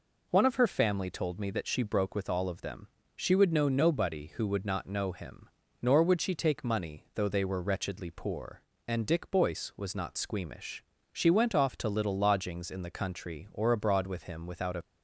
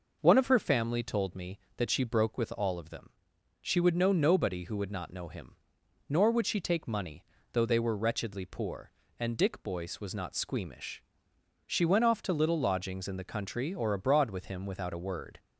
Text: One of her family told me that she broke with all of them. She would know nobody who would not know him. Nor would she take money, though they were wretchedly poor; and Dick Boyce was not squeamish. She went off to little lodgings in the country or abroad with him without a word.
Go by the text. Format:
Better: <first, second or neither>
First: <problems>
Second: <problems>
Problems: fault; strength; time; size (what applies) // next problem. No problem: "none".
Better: second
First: stops before "word"; at 14.8 s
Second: none